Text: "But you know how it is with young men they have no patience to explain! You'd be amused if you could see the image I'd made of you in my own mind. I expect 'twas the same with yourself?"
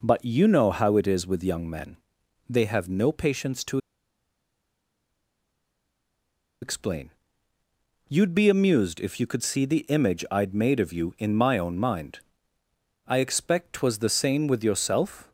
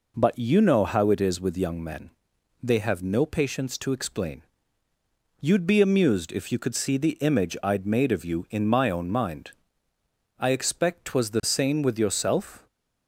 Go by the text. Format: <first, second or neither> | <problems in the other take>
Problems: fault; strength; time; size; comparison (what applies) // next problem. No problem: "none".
second | pauses between "men" and "they"; noticeable; at 1.9 s; 0.52 s long; noticeable in the second // pauses between "to" and "explain"; strong; at 3.7 s; 2.8 s long